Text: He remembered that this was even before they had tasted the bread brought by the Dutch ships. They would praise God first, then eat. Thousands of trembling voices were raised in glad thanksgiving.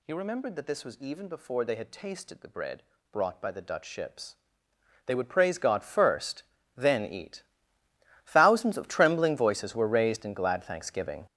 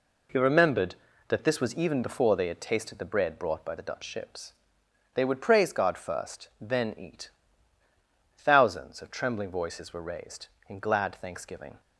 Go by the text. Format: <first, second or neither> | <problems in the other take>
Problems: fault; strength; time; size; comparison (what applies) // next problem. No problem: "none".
second | gets louder; strong; throughout; 10 dB // pauses between "bread" and "brought"; slight; at 2.8 s; 0.30 s long